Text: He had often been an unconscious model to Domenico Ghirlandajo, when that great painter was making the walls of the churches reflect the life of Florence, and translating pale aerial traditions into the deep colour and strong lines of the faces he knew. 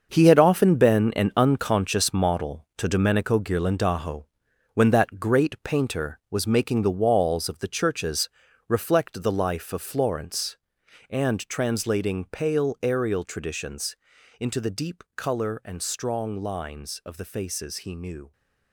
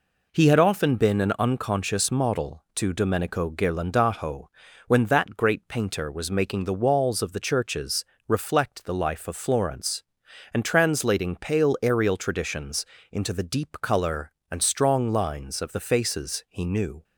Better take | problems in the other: second | gets quieter; strong; throughout; 10.5 dB // pauses between "churches" and "reflect"; at 8.2 s; 0.40 s long; slight in the second // pauses between "traditions" and "into"; at 13.9 s; 0.44 s long; slight in the second

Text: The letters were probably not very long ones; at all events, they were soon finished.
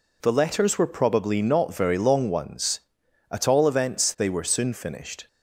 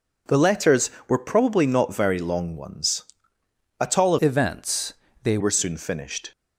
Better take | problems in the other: first | changes voice from "events" to "they"; from 4.1 to 5.3 s; 1.2 s long

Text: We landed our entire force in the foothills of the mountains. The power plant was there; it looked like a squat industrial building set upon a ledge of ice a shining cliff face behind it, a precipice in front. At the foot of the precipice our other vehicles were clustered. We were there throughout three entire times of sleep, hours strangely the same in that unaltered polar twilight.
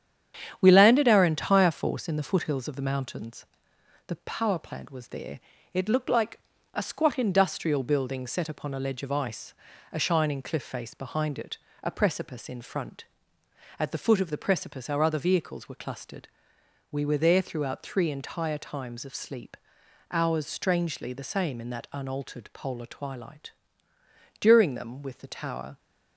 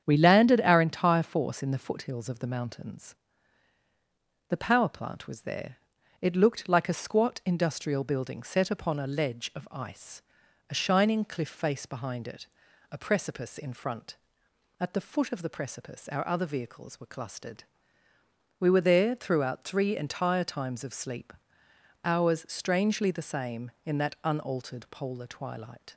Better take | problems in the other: second | starts louder than the rest; strong; until 1.6 s; 9 dB; strong in the second // pauses between "like" and "a"; slight; at 6.3 s; 0.34 s long // pauses between "ice" and "a"; at 9.5 s; 0.40 s long; noticeable in the second // goes on to say "During them with the tower"; from 24.4 s on; 1.3 s long

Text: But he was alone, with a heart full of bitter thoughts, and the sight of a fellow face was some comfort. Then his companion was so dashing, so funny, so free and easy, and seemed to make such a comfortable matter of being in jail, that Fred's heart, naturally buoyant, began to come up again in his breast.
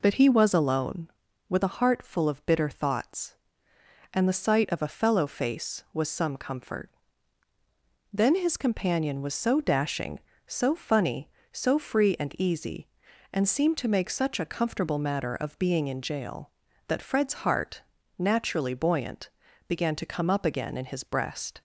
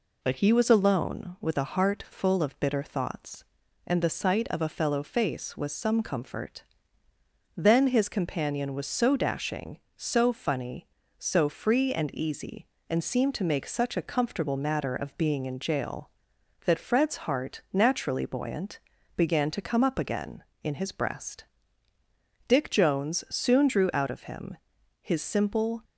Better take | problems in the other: first | goes on to say "Dick Jones soon drew out of him his simple"; strong; from 22.4 s on; 3.3 s long

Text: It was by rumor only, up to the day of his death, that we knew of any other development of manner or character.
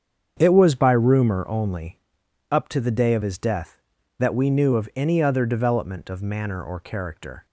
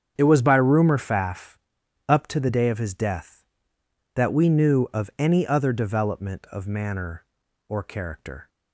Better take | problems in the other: first | starts louder than the rest; strong; until 1.1 s; 8 dB; strong in the first // says "faff" for "only"; at 0.9 s

